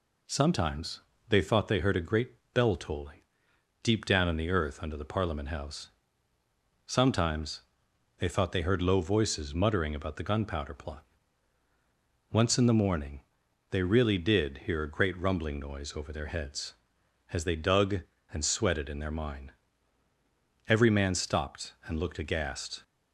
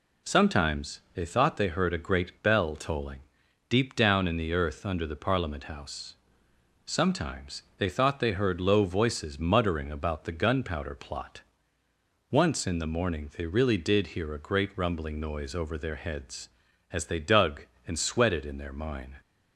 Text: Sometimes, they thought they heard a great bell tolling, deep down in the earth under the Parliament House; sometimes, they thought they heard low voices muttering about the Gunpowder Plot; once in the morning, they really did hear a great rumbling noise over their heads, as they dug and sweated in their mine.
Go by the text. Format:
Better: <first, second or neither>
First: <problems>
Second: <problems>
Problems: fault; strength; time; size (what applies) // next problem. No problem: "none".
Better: second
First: pauses between "great" and "bell"; slight; at 2.3 s; 0.20 s long // goes on to say "Every man stopped and looked aghast"; strong; from 20.6 s on; 2.1 s long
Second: none